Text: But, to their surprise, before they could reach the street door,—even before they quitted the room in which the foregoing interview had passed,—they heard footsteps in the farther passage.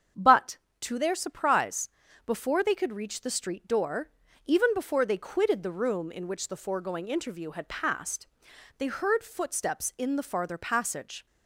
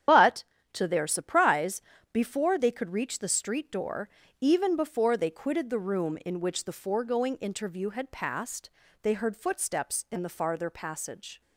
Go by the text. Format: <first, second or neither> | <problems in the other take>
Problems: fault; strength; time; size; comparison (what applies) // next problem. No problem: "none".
first | loses the start of "But"; at 0.0 s; 115 ms // starts louder than the rest; strong; until 1.3 s; 10 dB; strong in the first